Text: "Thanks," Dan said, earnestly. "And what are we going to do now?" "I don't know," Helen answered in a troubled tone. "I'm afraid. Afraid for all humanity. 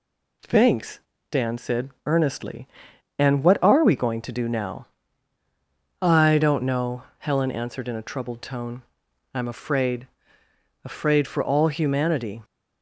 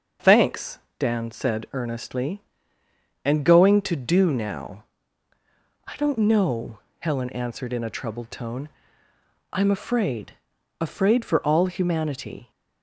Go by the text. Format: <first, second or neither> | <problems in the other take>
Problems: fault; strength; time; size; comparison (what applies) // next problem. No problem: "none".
first | starts louder than the rest; until 1.4 s; 6.5 dB // skips "what are we"; at 3.4 s